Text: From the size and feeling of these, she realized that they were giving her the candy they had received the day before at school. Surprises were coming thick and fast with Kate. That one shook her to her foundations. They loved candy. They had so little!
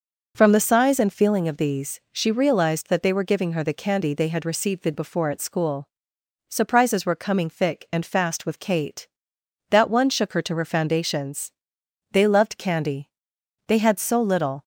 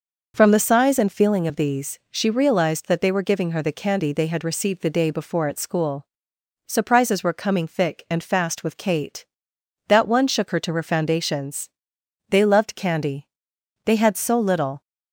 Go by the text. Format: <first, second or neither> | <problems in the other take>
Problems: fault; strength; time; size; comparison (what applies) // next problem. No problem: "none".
second | skips "day"; at 4.9 s